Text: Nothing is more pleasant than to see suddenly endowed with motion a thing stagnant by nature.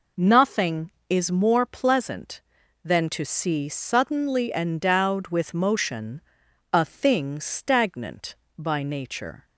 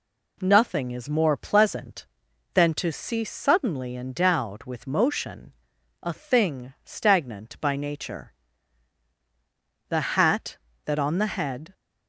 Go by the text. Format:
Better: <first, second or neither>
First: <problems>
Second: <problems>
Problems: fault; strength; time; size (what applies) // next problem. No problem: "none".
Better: first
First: pauses between "motion" and "a"; noticeable; at 6.2 s; 0.50 s long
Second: pauses between "motion" and "a"; noticeable; at 5.5 s; 0.48 s long // goes on to say "The hat that on the head"; strong; from 9.8 s on; 1.8 s long